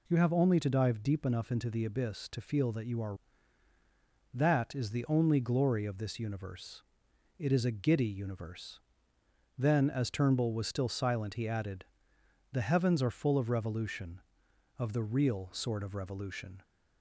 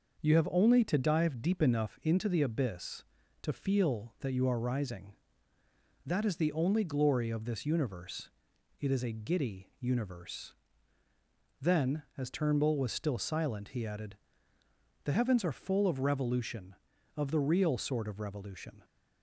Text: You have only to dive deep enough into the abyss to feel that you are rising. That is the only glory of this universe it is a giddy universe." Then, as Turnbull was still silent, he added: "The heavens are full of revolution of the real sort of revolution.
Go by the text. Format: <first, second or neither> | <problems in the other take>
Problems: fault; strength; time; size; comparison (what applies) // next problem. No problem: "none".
second | skips "rising"; at 3.7 s // pauses between "universe" and "it"; noticeable; at 6.8 s; 0.56 s long; noticeable in the second